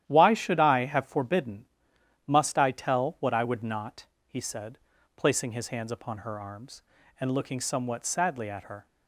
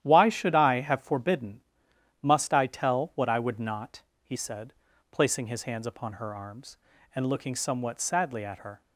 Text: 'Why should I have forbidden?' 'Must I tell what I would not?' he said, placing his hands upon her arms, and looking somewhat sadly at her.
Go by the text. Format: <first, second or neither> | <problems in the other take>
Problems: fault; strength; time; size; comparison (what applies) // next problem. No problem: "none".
neither | starts louder than the rest; strong; the same in both